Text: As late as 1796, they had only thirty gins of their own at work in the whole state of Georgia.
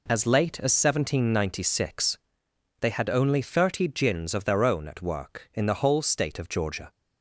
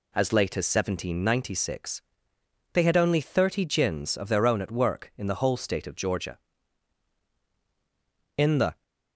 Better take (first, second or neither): first